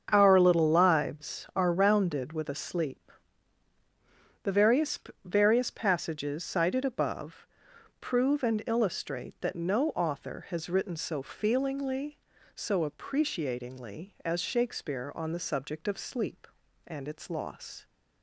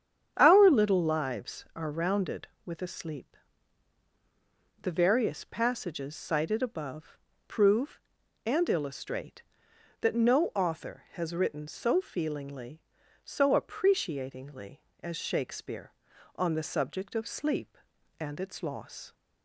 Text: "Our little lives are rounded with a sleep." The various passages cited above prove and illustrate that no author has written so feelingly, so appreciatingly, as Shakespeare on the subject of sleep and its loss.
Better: second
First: starts louder than the rest; strong; until 1.1 s; 7 dB // says "various" twice; at 5.2 s // pauses between "above" and "prove"; noticeable; at 7.4 s; 0.54 s long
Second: starts louder than the rest; strong; until 1.3 s; 8.5 dB // pauses between "above" and "prove"; slight; at 7.1 s; 0.28 s long

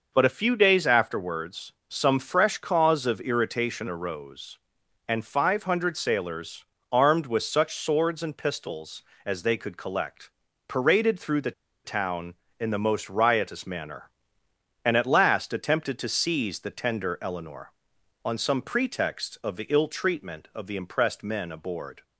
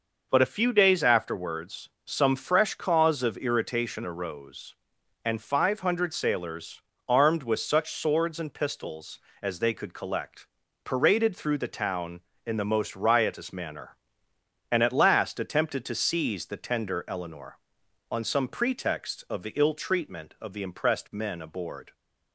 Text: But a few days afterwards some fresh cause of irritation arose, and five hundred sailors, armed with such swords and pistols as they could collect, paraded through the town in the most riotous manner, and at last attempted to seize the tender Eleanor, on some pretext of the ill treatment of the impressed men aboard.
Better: second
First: pauses between "afterwards" and "some"; slight; at 1.7 s; 0.16 s long // pauses between "the" and "town"; slight; at 11.5 s; 0.32 s long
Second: pauses between "afterwards" and "some"; slight; at 1.8 s; 0.16 s long

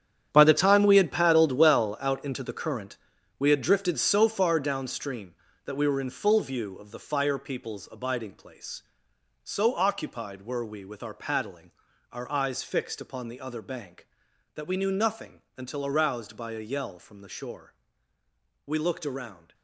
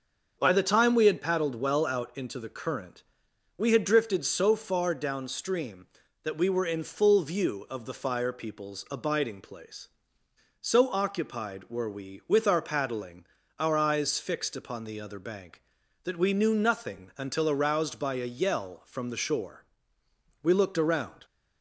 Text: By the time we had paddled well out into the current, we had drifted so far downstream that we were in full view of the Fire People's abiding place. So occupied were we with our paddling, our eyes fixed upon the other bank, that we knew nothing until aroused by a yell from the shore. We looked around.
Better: second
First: gets quieter; strong; throughout; 12.5 dB // starts louder than the rest; strong; until 1.3 s; 9 dB // pauses between "nothing" and "until"; slight; at 15.4 s; 0.16 s long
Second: starts louder than the rest; noticeable; until 1.3 s; 6 dB

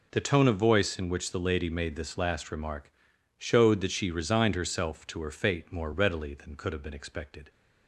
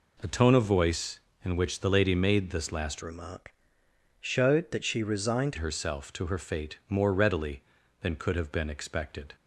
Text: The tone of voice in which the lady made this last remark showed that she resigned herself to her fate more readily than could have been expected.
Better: first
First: pauses between "remark" and "showed"; noticeable; at 2.9 s; 0.46 s long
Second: changes voice from "remark" to "resigned"; from 3.0 to 5.5 s; 2.5 s long // pauses between "remark" and "showed"; noticeable; at 3.5 s; 0.66 s long

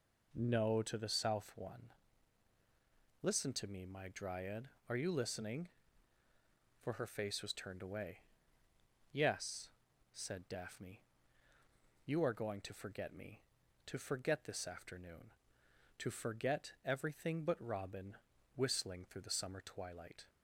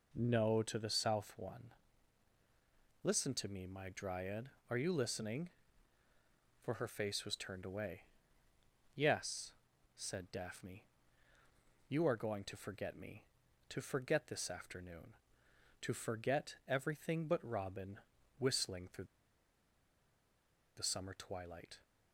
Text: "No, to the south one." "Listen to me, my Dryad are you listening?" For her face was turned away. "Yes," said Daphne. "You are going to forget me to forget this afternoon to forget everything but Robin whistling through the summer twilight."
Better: first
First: pauses between "Robin" and "whistling"; at 18.1 s; 0.38 s long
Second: pauses between "Robin" and "whistling"; at 18.0 s; 0.38 s long // pauses between "through" and "the"; strong; at 19.0 s; 1.7 s long

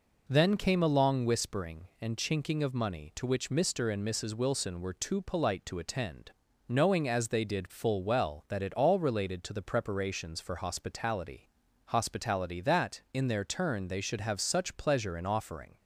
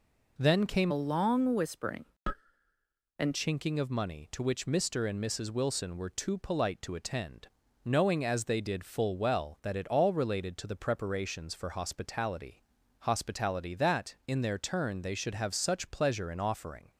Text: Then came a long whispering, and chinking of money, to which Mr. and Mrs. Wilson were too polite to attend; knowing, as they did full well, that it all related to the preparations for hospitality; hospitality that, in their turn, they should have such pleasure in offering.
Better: first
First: none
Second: changes voice from "a" to "and"; from 0.9 to 3.3 s; 2.4 s long

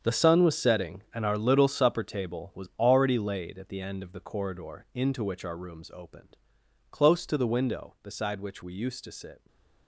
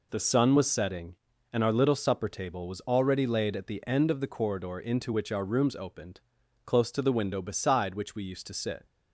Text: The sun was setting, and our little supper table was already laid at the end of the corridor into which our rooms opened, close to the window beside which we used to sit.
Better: second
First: gets quieter; strong; throughout; 12 dB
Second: none

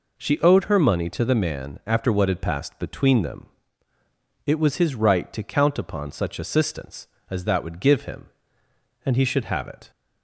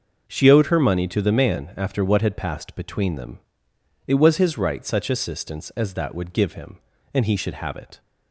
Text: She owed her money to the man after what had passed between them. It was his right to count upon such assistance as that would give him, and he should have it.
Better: first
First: none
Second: starts louder than the rest; noticeable; until 1.2 s; 6 dB // skips "to count upon"; at 4.8 s

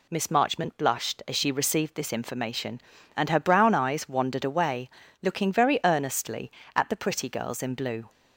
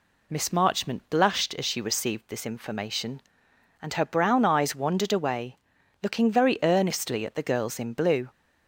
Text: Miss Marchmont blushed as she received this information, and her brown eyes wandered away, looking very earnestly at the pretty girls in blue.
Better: first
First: none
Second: skips "pretty"; at 7.4 s

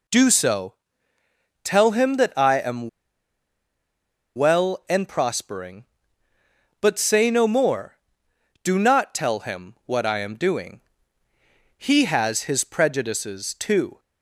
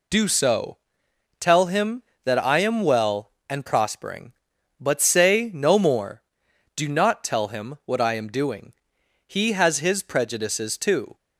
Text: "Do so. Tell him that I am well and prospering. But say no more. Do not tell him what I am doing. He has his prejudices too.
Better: second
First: pauses between "am" and "well"; strong; at 2.8 s; 1.4 s long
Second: none

